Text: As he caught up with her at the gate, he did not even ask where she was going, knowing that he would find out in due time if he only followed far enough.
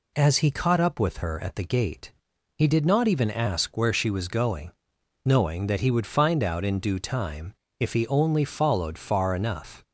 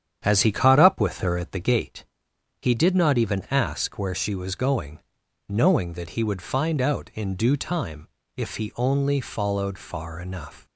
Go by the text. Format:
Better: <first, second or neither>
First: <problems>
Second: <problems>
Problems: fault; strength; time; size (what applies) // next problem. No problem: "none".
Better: first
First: pauses between "time" and "if"; slight; at 7.5 s; 0.24 s long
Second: starts louder than the rest; strong; until 1.9 s; 9 dB // pauses between "time" and "if"; slight; at 8.0 s; 0.30 s long